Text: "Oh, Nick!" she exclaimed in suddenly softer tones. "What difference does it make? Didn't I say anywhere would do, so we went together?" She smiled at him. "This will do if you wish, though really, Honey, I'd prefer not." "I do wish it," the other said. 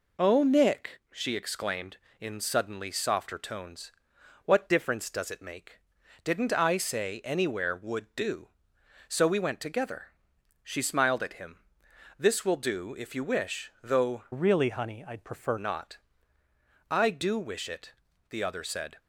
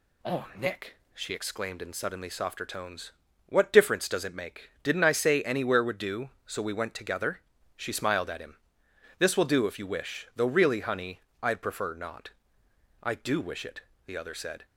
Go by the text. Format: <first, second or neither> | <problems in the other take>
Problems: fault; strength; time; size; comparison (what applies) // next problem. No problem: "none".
second | changes voice from "really" to "prefer"; from 14.3 to 15.5 s; 1.2 s long